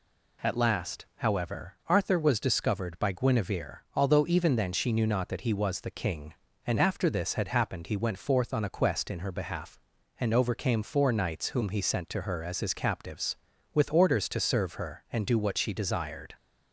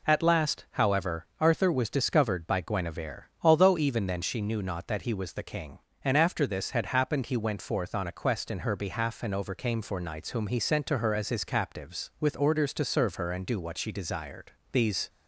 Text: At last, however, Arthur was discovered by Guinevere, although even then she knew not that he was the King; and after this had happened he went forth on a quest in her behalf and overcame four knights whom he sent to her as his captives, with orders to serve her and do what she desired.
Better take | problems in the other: first | goes on to say "These"; slight; from 14.7 s on; 0.36 s long

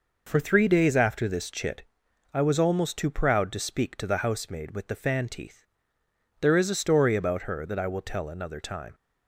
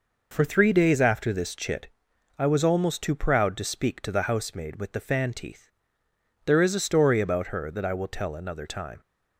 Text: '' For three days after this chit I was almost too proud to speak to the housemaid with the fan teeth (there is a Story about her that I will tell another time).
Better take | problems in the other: neither | pauses between "chit" and "I"; noticeable; the same in both

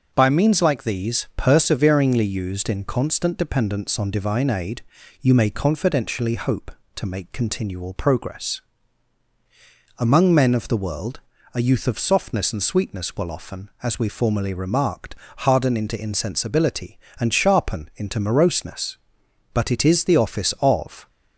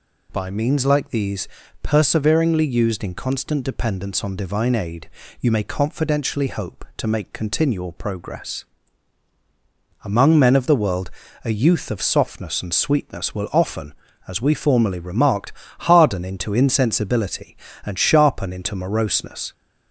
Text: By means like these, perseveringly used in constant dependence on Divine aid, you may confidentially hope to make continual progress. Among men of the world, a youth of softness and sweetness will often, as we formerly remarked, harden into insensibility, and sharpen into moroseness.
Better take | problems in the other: second | goes on to say "But it is the office of"; from 19.5 s on; 1.5 s long

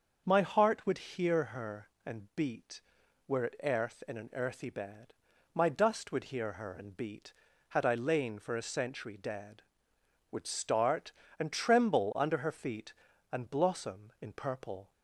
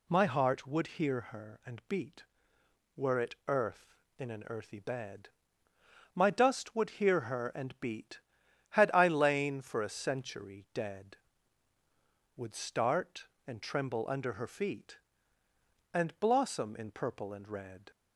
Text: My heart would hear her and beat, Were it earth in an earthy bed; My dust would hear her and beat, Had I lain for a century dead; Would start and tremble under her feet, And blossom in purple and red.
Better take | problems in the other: second | starts louder than the rest; until 1.2 s; 6.5 dB // stops before "and red"; at 14.9 s

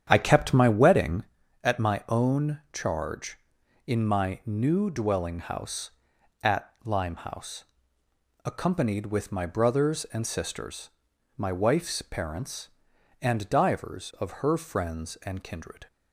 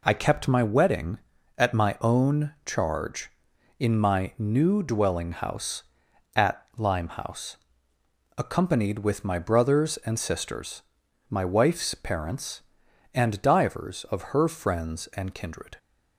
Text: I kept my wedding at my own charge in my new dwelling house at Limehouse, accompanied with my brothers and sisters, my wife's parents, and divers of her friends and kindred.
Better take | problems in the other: second | starts louder than the rest; strong; until 1.3 s; 9 dB

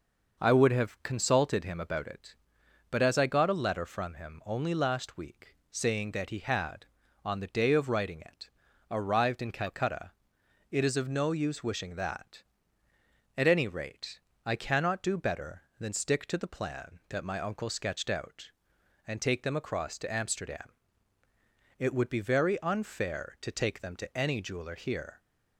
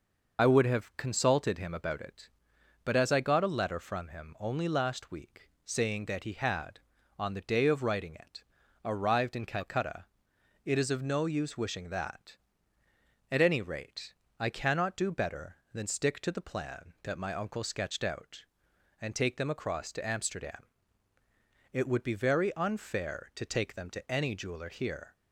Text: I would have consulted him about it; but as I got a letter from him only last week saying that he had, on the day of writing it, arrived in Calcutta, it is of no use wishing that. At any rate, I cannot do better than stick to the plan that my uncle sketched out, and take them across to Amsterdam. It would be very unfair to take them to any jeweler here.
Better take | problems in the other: first | loses the start of "I"; at 0.3 s; 55 ms // pauses between "week" and "saying"; slight; at 5.4 s; 0.16 s long; slight in the first

